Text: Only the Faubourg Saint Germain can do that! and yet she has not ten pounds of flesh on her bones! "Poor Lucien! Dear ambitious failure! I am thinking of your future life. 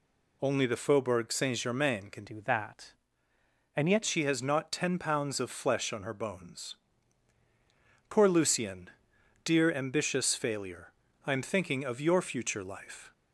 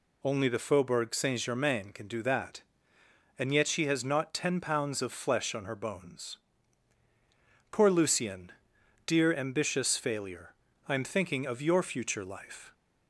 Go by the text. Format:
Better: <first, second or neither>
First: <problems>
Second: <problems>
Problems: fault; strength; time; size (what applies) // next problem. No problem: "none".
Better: second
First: changes voice from "do" to "yet"; from 2.2 to 4.0 s; 1.8 s long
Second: none